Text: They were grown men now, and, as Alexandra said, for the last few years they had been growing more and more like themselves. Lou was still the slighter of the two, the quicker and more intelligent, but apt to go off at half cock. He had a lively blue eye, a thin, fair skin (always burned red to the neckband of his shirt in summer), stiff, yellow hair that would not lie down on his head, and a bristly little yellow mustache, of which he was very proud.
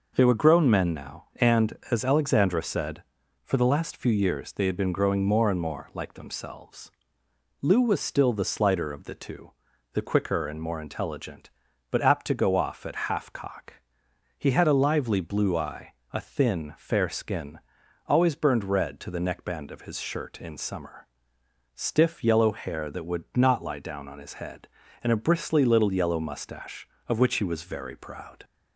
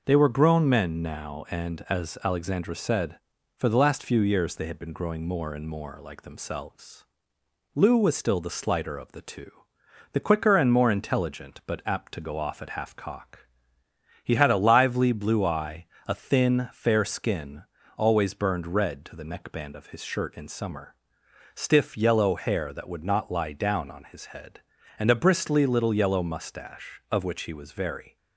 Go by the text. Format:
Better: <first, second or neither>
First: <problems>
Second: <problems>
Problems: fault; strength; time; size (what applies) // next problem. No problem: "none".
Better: first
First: none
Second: stops before "proud"; at 28.1 s